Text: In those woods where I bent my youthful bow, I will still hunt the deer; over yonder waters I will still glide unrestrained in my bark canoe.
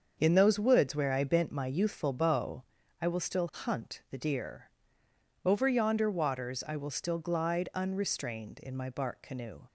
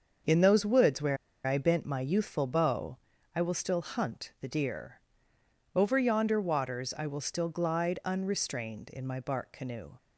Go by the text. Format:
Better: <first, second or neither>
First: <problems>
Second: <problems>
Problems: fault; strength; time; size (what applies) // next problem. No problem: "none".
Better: first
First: starts louder than the rest; until 1.1 s; 6.5 dB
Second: starts louder than the rest; until 1.5 s; 6.5 dB // pauses between "where" and "I"; slight; at 1.1 s; 0.30 s long